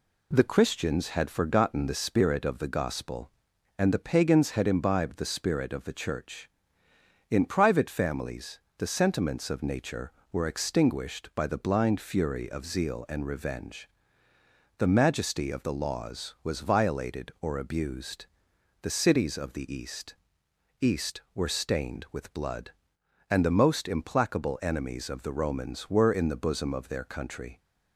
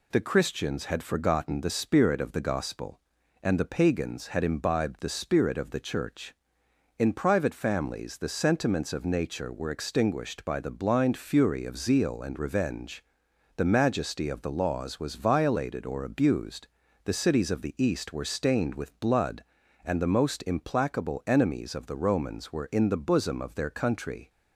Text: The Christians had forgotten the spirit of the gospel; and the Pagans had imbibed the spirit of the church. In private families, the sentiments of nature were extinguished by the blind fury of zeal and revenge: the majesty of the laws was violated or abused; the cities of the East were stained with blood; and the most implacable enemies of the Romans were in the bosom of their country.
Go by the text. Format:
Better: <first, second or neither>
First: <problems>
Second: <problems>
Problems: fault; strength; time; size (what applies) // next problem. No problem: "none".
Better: second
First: says "East" twice; at 20.7 s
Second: none